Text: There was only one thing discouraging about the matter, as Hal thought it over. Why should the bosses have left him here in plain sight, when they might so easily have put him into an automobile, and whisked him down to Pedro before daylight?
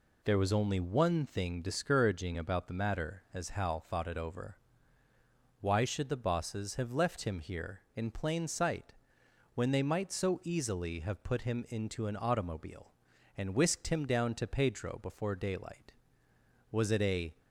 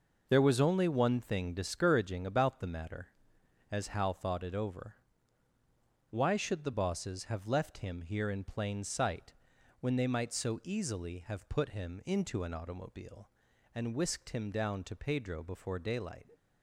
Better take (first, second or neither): second